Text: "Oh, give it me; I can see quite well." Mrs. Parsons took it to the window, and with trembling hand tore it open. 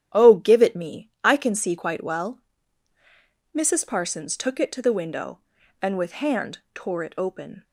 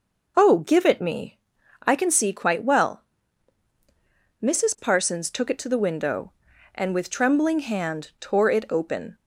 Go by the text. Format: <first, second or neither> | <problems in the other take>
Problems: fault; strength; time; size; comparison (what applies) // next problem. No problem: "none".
second | starts louder than the rest; strong; until 1.2 s; 10 dB // skips "trembling"; at 6.2 s